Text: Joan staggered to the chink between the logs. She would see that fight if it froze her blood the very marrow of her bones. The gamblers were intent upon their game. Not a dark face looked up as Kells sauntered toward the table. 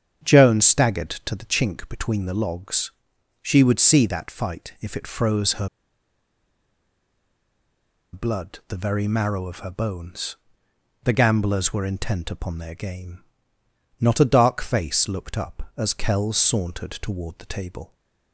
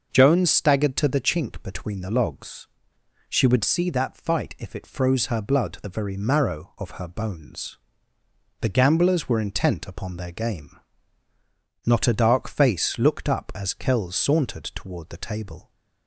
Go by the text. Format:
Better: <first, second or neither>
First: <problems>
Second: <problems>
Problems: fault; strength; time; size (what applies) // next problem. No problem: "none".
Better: second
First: starts louder than the rest; strong; until 1.3 s; 8 dB // pauses between "her" and "blood"; strong; at 5.6 s; 2.4 s long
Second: starts louder than the rest; noticeable; until 1.1 s; 6 dB